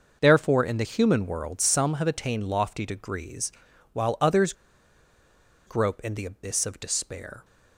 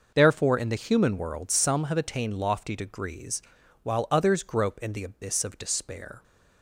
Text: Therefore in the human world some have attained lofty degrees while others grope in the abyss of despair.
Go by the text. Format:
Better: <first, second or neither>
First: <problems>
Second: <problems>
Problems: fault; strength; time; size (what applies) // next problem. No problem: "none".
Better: second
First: pauses between "degrees" and "while"; at 3.5 s; 0.42 s long // pauses between "others" and "grope"; at 4.5 s; 1.1 s long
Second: pauses between "degrees" and "while"; at 3.4 s; 0.42 s long